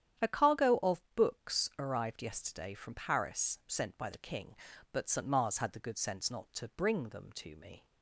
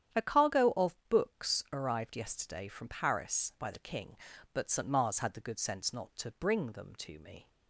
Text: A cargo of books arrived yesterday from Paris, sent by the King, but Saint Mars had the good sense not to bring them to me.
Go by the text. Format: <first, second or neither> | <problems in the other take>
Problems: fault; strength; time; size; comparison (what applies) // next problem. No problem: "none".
first | starts louder than the rest; strong; until 1.2 s; 9.5 dB; strong in the first // skips "sent"; at 3.5 s